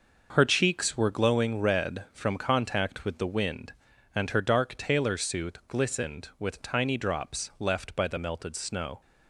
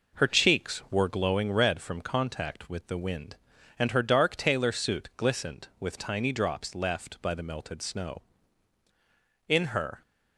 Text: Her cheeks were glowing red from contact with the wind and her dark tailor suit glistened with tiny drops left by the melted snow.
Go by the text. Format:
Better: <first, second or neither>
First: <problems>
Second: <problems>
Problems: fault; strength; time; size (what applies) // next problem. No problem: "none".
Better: first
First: none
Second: goes on to say "In her"; from 9.4 s on; 0.54 s long